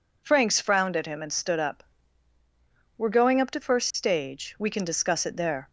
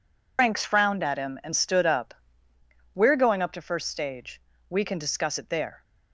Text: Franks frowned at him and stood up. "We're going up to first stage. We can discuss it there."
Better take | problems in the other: first | loses the start of "Franks"; at 0.3 s; 110 ms

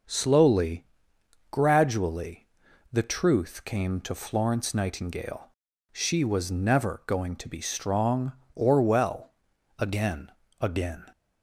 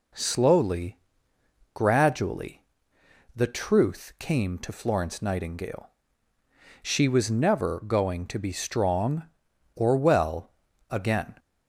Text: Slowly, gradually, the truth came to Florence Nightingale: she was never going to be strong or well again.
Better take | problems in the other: second | pauses between "well" and "again"; noticeable; at 9.3 s; 0.48 s long; also in the second // says "again" twice; at 10.6 s

